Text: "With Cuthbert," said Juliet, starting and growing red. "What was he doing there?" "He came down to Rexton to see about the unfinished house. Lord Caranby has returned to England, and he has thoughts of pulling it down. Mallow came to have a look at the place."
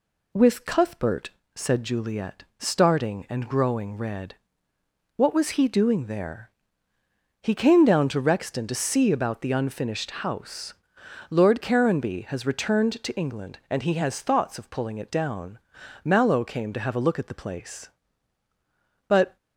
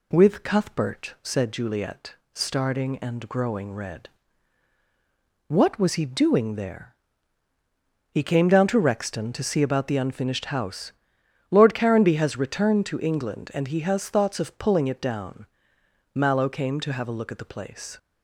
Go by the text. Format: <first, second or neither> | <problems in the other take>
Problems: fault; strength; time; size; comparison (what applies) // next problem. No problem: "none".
second | goes on to say "But"; slight; from 19.0 s on; 0.28 s long